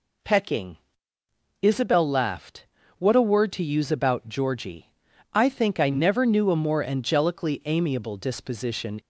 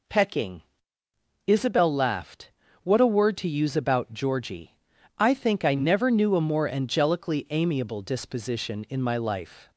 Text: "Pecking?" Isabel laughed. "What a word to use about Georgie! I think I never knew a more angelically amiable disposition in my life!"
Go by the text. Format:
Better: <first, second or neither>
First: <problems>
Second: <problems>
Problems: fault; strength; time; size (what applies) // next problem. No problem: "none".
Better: second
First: stops before "in my life"; at 8.9 s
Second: none